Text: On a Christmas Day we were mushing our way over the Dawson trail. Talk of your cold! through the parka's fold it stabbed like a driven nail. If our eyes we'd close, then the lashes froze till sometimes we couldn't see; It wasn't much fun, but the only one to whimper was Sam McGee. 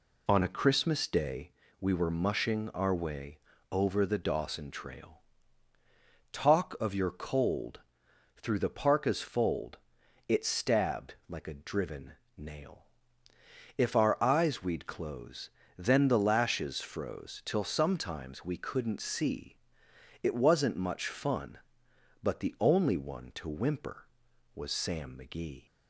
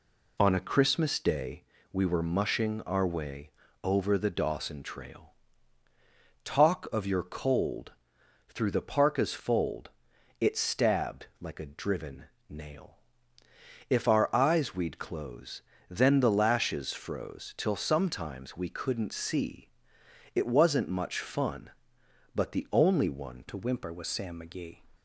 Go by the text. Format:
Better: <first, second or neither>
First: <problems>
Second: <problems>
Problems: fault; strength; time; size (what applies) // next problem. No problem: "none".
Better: first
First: pauses between "Day" and "we"; slight; at 1.5 s; 0.28 s long // pauses between "way" and "over"; slight; at 3.3 s; 0.32 s long // pauses between "fold" and "it"; noticeable; at 9.7 s; 0.50 s long // pauses between "stabbed" and "like"; slight; at 11.1 s; 0.16 s long // pauses between "driven" and "nail"; slight; at 12.1 s; 0.22 s long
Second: pauses between "Day" and "we"; slight; at 1.6 s; 0.28 s long // pauses between "way" and "over"; slight; at 3.4 s; 0.32 s long // pauses between "fold" and "it"; noticeable; at 9.8 s; 0.50 s long // pauses between "stabbed" and "like"; slight; at 11.2 s; 0.16 s long // pauses between "driven" and "nail"; slight; at 12.2 s; 0.22 s long // changes voice at "to"; from 23.4 s on; 1.4 s long